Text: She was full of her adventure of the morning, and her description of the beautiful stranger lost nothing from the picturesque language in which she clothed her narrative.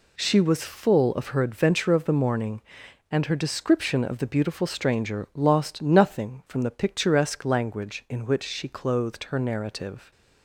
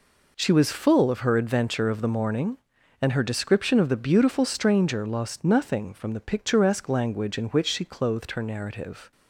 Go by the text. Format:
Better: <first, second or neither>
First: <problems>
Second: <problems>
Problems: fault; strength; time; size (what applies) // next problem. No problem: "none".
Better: neither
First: none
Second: none